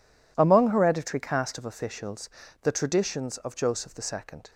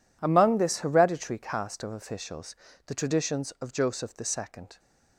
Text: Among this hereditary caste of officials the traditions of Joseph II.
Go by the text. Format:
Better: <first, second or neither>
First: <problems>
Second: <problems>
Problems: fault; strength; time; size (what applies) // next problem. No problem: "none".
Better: second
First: skips "this"; at 0.7 s // pauses between "officials" and "the"; slight; at 2.2 s; 0.34 s long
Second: pauses between "officials" and "the"; slight; at 2.5 s; 0.30 s long